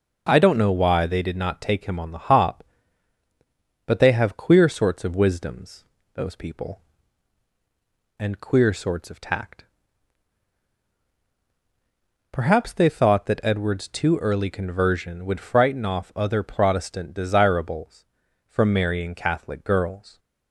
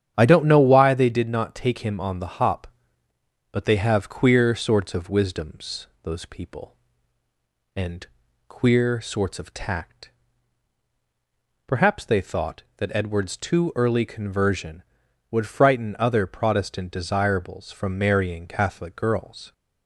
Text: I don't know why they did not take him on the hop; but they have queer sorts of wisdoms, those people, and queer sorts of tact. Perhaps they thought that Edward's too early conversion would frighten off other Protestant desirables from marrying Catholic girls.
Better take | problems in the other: first | starts louder than the rest; strong; until 1.1 s; 9.5 dB // pauses between "and" and "queer"; at 8.0 s; 0.42 s long // skips "off"; at 15.9 s

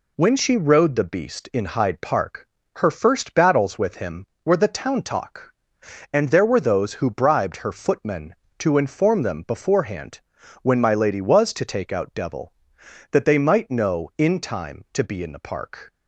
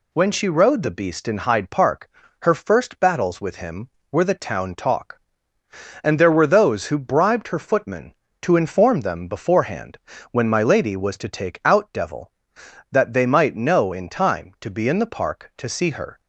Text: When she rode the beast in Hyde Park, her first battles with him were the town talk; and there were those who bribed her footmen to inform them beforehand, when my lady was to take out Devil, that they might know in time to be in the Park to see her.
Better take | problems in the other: second | stops before "to see her"; at 15.9 s

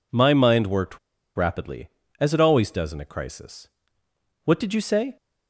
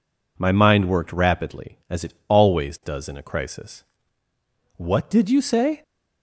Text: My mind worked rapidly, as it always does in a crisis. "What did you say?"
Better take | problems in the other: second | pauses between "worked" and "rapidly"; at 0.9 s; 0.38 s long

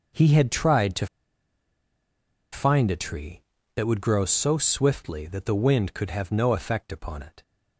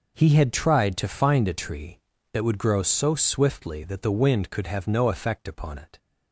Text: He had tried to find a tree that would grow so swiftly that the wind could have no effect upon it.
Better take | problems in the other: second | pauses between "to" and "find"; strong; at 1.0 s; 1.4 s long

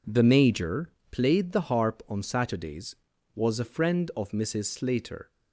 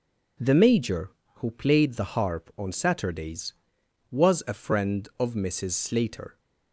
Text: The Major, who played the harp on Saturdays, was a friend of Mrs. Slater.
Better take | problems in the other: second | skips "who"; at 1.0 s

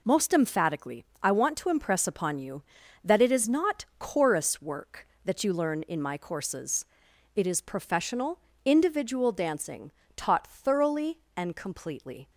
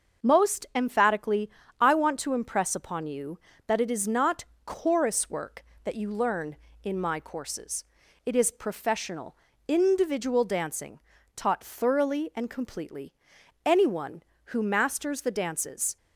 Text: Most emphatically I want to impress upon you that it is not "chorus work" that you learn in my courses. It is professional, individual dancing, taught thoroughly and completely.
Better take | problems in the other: first | starts louder than the rest; until 1.3 s; 6.5 dB // pauses between "emphatically" and "I"; slight; at 1.4 s; 0.30 s long; slight in the first // pauses between "not" and "chorus"; slight; at 4.4 s; 0.22 s long // goes on to say "Anyone who masters the dances"; strong; from 13.6 s on; 2.3 s long

